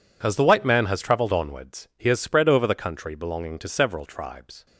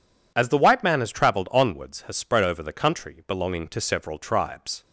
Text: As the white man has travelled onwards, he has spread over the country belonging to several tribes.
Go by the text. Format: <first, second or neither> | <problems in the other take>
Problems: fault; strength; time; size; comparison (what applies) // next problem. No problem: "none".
first | skips "he"; at 2.0 s